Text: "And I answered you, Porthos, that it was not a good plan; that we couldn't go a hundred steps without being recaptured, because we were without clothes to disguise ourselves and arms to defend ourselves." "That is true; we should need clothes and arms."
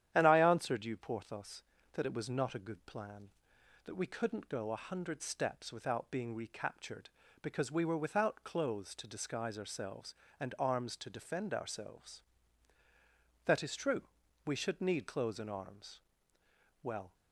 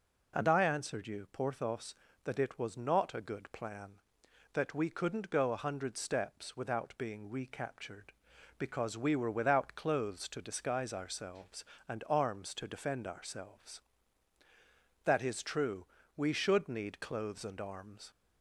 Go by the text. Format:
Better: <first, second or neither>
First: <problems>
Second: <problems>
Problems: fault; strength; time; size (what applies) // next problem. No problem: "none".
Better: second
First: starts louder than the rest; strong; until 1.1 s; 10.5 dB // goes on to say "Well"; slight; from 16.8 s on; 0.30 s long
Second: none